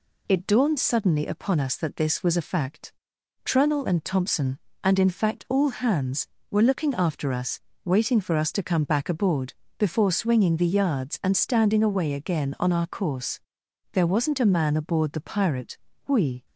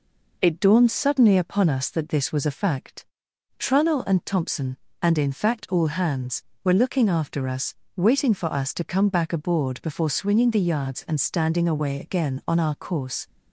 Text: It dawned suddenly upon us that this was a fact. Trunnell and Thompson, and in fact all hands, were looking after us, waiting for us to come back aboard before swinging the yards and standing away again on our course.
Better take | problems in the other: second | pauses between "aboard" and "before"; slight; at 9.5 s; 0.24 s long // goes on to say "There wasn't a man aboard the Pirate we"; strong; from 13.9 s on; 2.5 s long

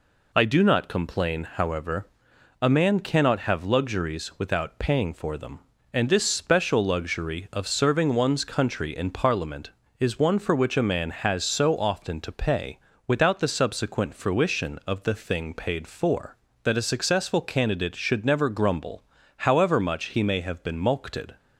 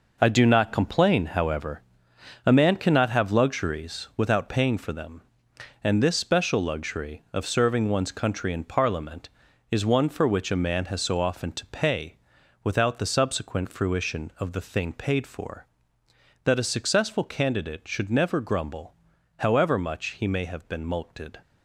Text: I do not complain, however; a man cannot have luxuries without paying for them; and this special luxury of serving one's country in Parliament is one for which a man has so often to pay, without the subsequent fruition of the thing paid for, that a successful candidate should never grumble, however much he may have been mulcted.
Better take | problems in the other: first | gets quieter; strong; throughout; 8.5 dB

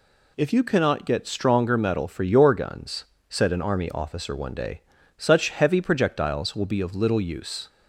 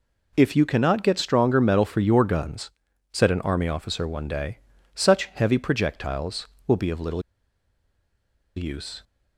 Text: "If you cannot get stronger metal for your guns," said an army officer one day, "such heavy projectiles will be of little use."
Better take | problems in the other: first | pauses between "little" and "use"; strong; at 7.2 s; 1.3 s long

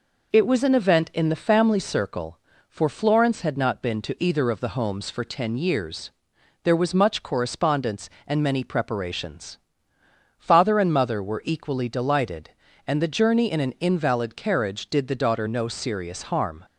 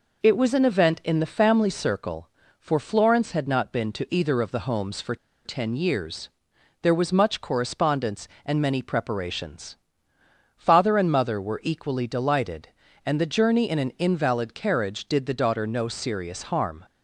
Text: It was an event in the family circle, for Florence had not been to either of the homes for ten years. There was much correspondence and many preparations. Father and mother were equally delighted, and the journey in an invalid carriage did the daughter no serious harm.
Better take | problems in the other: first | pauses between "for" and "ten"; slight; at 5.1 s; 0.30 s long

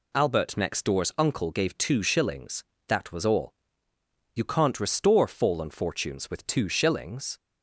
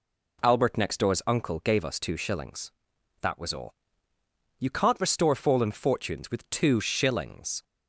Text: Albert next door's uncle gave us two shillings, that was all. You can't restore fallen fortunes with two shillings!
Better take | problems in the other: second | skips "us"; at 1.7 s

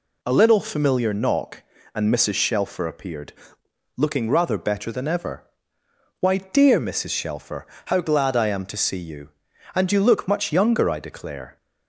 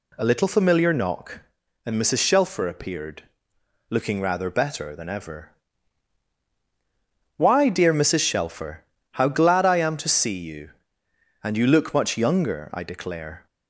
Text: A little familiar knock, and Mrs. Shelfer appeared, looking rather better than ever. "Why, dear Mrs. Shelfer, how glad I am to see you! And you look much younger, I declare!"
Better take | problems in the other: neither | none

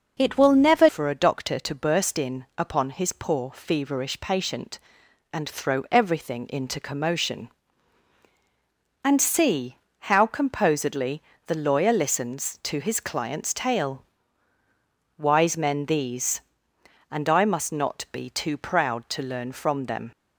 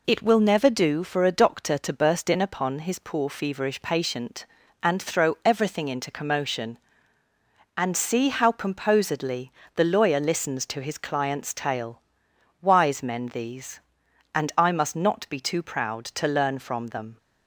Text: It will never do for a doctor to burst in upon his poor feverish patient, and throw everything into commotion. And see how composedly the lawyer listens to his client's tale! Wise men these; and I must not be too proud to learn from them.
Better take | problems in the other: second | skips "do"; at 0.8 s // pauses between "see" and "how"; slight; at 9.7 s; 0.24 s long // pauses between "composedly" and "the"; slight; at 11.2 s; 0.24 s long; slight in the second

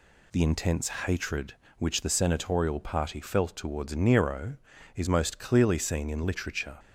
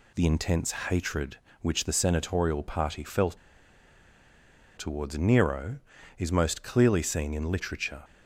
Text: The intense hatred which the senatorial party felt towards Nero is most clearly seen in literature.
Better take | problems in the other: first | pauses between "felt" and "towards"; strong; at 3.3 s; 1.4 s long

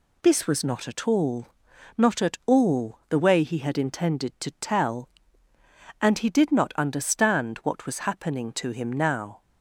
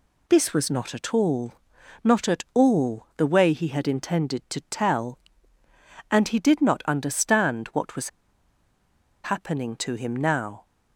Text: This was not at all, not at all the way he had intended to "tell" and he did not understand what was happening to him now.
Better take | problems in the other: first | pauses between "was" and "happening"; at 8.0 s; 1.1 s long

